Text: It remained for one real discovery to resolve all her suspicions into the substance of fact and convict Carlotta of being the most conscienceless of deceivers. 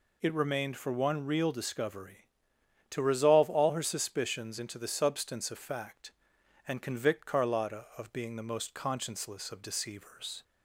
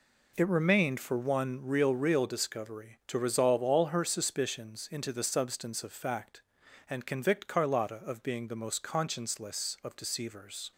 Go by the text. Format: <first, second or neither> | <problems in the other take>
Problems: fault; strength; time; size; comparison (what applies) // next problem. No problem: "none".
first | says "real" twice; at 1.9 s